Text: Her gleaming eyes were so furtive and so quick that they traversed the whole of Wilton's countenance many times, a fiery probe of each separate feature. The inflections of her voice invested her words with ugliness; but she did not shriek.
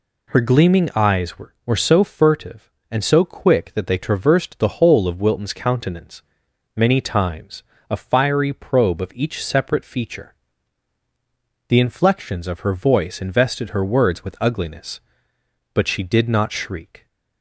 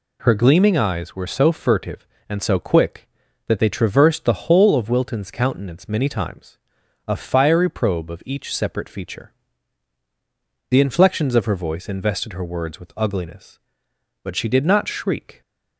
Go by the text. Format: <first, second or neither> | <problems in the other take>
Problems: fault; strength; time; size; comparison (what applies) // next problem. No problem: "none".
second | says "were" twice; at 1.6 s // pauses between "countenance" and "many"; noticeable; at 6.2 s; 0.56 s long